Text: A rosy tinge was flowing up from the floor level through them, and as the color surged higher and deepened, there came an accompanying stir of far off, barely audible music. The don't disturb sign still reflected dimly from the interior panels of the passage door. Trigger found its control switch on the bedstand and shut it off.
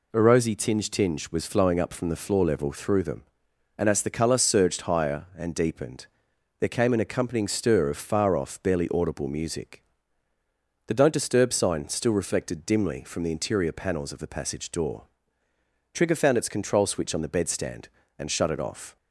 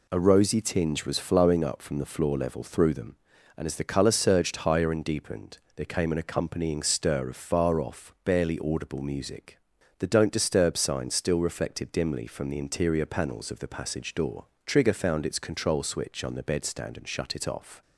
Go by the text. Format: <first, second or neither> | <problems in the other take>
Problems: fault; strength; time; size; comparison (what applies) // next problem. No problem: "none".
second | says "tinge" twice; at 0.9 s